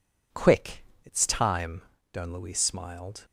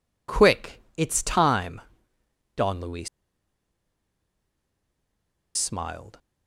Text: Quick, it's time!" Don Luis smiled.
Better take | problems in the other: first | pauses between "Luis" and "smiled"; strong; at 3.0 s; 2.4 s long

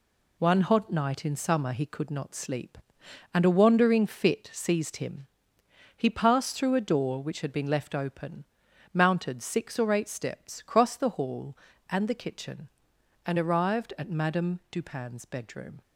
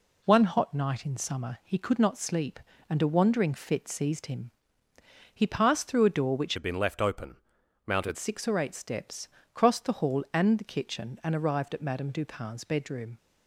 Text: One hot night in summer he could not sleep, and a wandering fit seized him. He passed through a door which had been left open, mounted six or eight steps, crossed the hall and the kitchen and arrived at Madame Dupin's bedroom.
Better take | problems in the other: first | changes voice from "had" to "mounted"; from 6.5 to 8.1 s; 1.6 s long

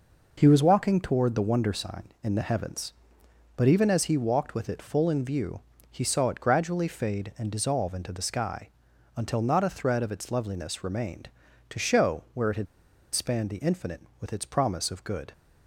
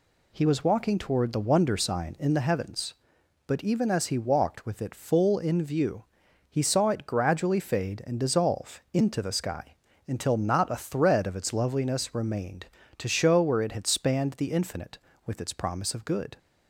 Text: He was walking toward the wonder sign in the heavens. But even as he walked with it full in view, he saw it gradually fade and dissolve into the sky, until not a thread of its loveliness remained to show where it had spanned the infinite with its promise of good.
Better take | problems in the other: second | pauses between "had" and "spanned"; noticeable; at 12.6 s; 0.47 s long

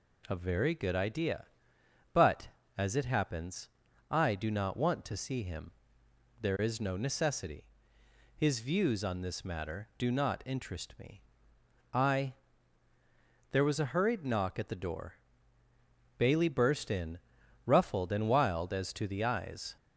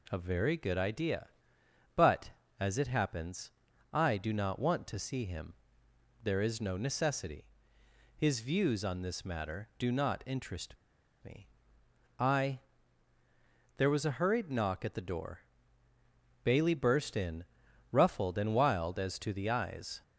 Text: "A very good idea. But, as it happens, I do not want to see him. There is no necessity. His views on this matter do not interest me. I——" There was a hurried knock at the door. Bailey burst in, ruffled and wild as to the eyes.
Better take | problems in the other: first | pauses between "interest" and "me"; noticeable; at 10.7 s; 0.48 s long

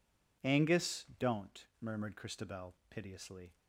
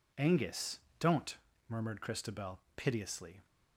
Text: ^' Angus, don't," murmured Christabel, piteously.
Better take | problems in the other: neither | none

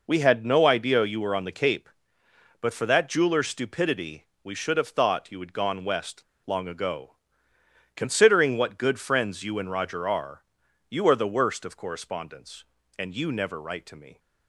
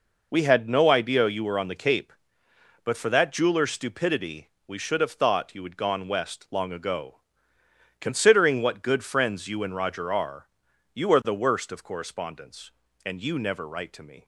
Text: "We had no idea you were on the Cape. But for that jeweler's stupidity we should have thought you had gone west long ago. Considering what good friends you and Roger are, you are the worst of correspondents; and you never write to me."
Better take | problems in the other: second | pauses between "stupidity" and "we"; slight; at 4.2 s; 0.18 s long; slight in the second // pauses between "west" and "long"; slight; at 6.2 s; 0.21 s long

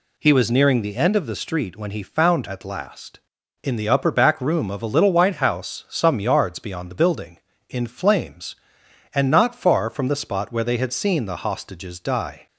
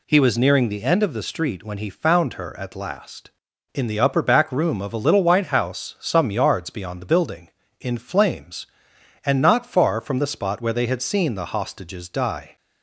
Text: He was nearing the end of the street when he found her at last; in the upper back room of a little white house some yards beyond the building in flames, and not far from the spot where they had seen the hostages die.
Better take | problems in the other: second | skips "her"; at 2.4 s

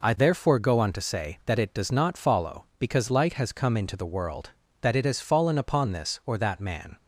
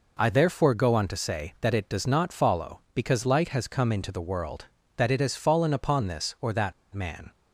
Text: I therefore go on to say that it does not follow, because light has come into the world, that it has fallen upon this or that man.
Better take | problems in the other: first | pauses between "that" and "man"; slight; at 6.7 s; 0.19 s long

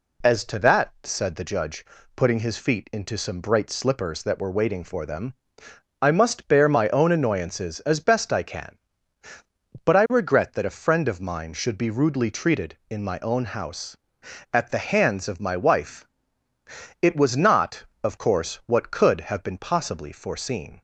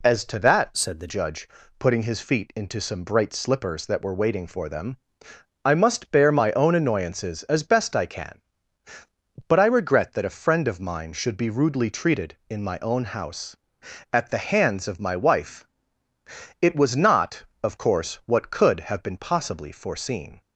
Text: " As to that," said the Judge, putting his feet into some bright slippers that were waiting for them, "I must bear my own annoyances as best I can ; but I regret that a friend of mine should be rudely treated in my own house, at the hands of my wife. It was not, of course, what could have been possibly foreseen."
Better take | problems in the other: first | changes voice from "said" to "the"; from 0.7 to 1.0 s; 0.3 s long

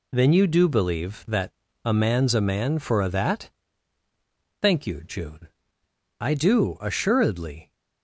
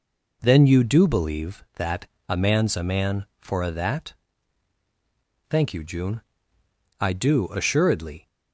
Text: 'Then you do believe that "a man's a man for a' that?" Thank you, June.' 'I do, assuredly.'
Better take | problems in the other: neither | pauses between "that" and "a"; slight; the same in both

